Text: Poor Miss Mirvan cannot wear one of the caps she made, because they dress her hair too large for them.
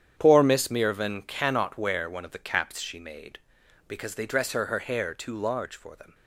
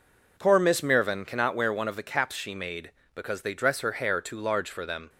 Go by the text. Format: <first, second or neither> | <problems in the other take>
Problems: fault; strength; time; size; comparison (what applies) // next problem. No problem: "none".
second | starts louder than the rest; strong; until 1.1 s; 9 dB // says "her" twice; at 4.6 s